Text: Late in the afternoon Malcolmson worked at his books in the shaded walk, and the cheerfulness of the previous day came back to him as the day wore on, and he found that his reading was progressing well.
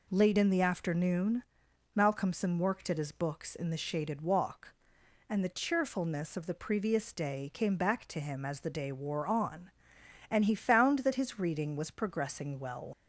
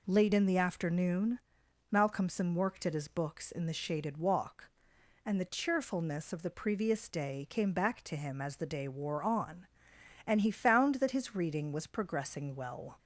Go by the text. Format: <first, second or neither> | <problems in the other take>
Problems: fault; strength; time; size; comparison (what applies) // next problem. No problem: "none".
second | pauses between "afternoon" and "Malcolmson"; noticeable; at 1.4 s; 0.50 s long; noticeable in the second // leaves "well" unfinished; at 12.9 s; 85 ms